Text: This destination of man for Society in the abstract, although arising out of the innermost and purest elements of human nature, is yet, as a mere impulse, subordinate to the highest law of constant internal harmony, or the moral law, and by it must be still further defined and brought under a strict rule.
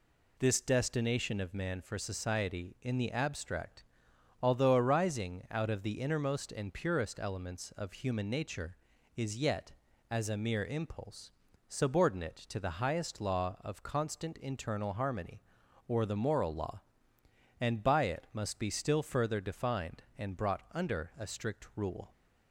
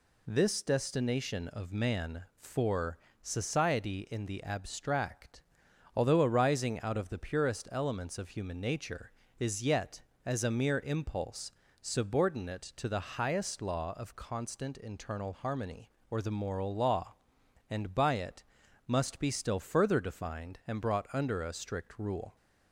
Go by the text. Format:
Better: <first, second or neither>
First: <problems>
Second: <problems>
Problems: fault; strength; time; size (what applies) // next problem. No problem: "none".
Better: first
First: none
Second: pauses between "for" and "Society"; slight; at 2.9 s; 0.26 s long // skips "innermost and"; at 7.1 s // pauses between "it" and "must"; at 18.4 s; 0.44 s long